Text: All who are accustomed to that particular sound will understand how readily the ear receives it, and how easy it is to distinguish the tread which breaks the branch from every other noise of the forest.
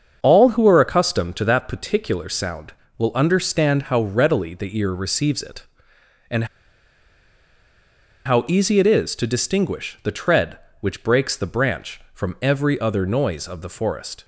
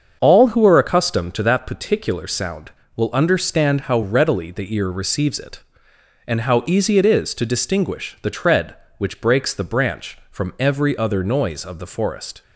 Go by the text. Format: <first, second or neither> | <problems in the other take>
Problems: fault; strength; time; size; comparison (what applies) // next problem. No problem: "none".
second | starts louder than the rest; until 1.2 s; 7 dB; also in the second // pauses between "and" and "how"; strong; at 6.4 s; 1.8 s long